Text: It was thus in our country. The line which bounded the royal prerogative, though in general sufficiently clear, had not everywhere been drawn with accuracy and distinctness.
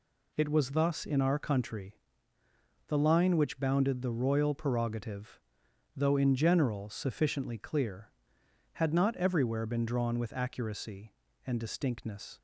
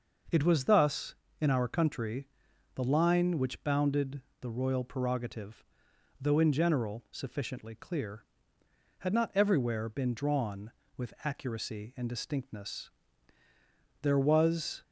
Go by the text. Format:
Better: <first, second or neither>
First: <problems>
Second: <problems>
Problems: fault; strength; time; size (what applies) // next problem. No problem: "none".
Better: first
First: none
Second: pauses between "bounded" and "the"; slight; at 4.2 s; 0.20 s long // goes on to say "There was"; noticeable; from 14.0 s on; 0.80 s long